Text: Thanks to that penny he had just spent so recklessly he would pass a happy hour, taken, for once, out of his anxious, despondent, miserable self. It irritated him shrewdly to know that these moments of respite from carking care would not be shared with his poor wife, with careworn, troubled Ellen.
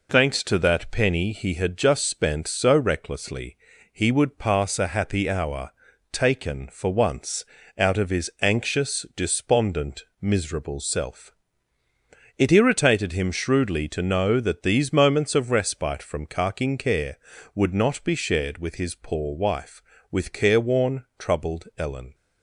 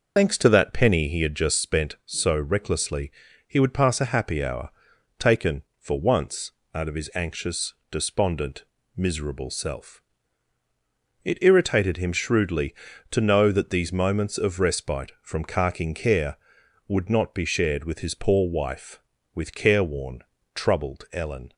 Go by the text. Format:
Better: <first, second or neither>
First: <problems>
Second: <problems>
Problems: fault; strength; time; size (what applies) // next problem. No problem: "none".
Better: first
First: pauses between "recklessly" and "he"; slight; at 3.5 s; 0.36 s long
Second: loses the start of "Thanks"; at 0.1 s; 80 ms // pauses between "recklessly" and "he"; slight; at 3.1 s; 0.36 s long